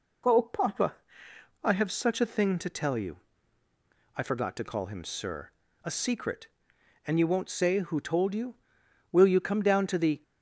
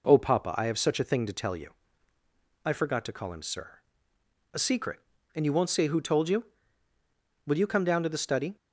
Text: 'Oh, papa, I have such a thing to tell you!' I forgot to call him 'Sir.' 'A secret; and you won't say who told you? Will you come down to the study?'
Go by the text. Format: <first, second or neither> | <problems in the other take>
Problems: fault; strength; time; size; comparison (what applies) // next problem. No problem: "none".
second | stops before "study"; at 10.2 s